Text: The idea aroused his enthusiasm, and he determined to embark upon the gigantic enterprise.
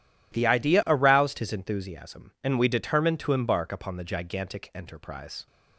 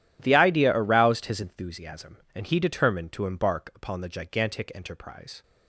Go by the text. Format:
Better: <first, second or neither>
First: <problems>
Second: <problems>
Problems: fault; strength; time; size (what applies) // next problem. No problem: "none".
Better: second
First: says "we" for "he"; at 2.5 s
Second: none